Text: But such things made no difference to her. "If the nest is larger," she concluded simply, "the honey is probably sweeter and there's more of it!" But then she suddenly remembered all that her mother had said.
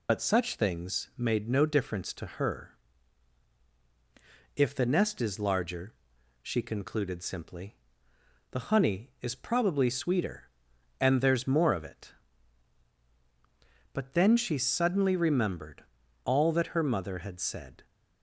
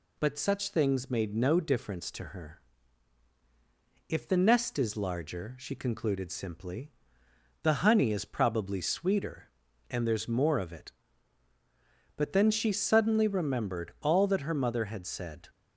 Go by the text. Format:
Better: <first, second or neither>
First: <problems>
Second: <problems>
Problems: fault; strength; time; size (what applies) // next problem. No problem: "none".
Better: second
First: loses the start of "But"; at 0.0 s; 70 ms // pauses between "remembered" and "all"; at 15.8 s; 0.40 s long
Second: none